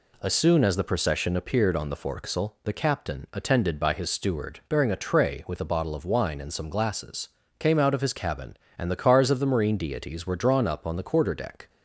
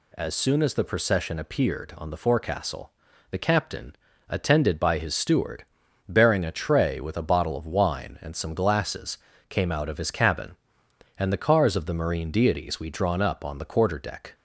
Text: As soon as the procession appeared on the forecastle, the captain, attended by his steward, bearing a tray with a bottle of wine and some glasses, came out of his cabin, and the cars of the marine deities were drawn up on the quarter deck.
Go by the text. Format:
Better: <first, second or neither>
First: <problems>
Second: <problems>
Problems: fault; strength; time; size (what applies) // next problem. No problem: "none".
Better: first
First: none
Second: says "we" for "were"; at 12.7 s